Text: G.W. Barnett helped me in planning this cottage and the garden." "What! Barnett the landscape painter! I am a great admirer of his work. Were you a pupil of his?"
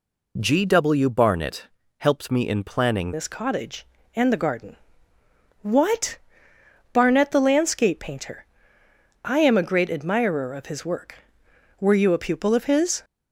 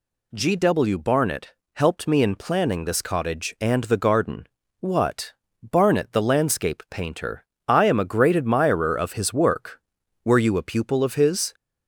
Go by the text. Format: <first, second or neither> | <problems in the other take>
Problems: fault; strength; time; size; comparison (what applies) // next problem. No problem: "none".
second | pauses between "Barnett" and "helped"; slight; at 1.6 s; 0.28 s long; slight in the second // changes voice at "this"; from 3.1 s on; 9.9 s long